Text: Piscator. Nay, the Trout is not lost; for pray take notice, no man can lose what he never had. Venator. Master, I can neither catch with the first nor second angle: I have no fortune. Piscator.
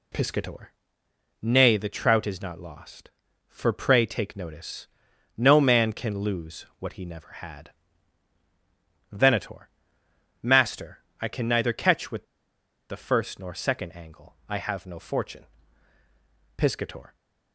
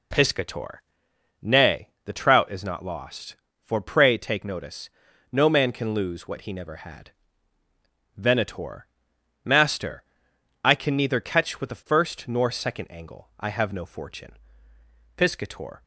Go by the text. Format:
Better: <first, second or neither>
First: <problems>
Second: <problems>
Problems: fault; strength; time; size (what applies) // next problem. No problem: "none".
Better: second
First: pauses between "with" and "the"; noticeable; at 12.2 s; 0.64 s long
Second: none